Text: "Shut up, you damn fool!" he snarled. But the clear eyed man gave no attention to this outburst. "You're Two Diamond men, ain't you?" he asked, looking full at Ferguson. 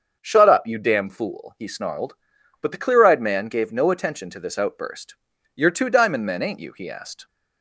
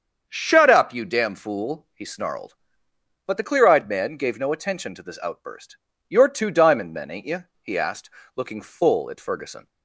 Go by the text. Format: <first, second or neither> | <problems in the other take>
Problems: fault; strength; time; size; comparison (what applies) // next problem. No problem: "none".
second | starts louder than the rest; until 1.2 s; 7 dB; strong in the second // stops before "looking full at Ferguson"; at 7.2 s